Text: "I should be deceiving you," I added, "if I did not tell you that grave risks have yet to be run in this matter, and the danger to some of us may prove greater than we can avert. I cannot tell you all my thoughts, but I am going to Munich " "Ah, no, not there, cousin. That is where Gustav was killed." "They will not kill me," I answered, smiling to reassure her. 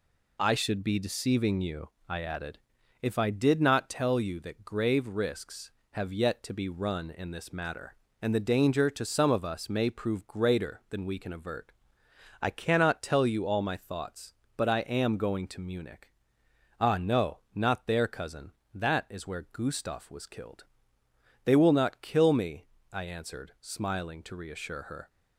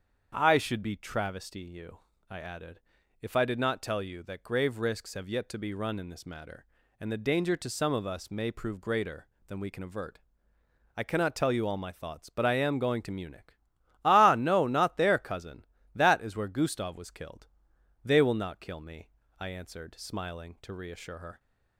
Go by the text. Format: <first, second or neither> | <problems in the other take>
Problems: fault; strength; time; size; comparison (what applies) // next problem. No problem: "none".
first | starts louder than the rest; strong; until 1.3 s; 7.5 dB // says "travesty" for "deceiving"; at 0.9 s